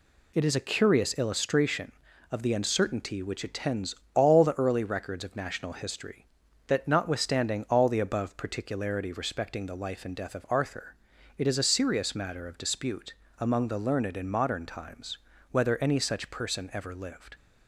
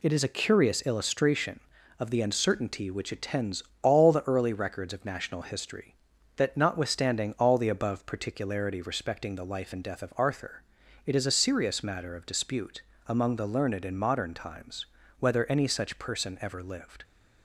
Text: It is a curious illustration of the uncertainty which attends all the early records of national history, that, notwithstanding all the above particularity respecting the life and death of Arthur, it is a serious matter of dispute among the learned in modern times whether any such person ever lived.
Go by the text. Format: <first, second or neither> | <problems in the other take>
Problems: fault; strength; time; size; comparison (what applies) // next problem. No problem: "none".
neither | pauses between "attends" and "all"; slight; the same in both // pauses between "dispute" and "among"; slight; the same in both // pauses between "times" and "whether"; slight; the same in both